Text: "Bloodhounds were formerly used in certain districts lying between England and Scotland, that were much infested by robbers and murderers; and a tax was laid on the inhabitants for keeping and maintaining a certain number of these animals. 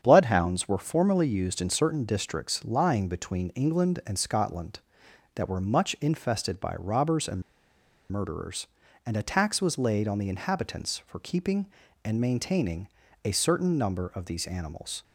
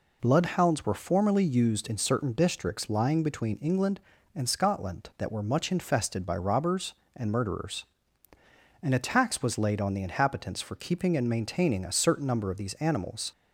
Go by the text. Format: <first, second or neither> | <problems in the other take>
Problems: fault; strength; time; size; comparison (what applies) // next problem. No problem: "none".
second | starts louder than the rest; strong; until 1.0 s; 8 dB // pauses between "and" and "murderers"; noticeable; at 7.4 s; 0.68 s long // pauses between "maintaining" and "a"; at 12.8 s; 0.38 s long